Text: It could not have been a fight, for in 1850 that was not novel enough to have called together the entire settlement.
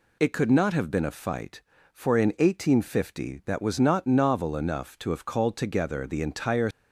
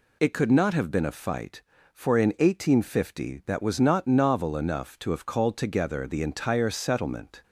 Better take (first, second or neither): second